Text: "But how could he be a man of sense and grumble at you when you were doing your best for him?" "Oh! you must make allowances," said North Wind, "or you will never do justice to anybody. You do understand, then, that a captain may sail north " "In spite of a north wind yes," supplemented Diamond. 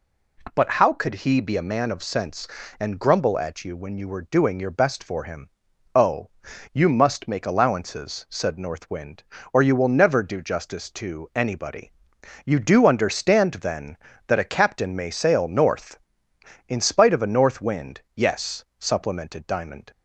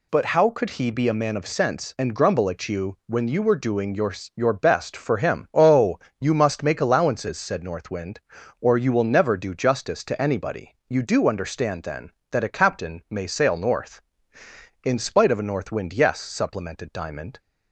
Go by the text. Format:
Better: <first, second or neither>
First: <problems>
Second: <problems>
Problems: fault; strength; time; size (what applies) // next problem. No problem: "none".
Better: first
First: none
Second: says "your" twice; at 4.3 s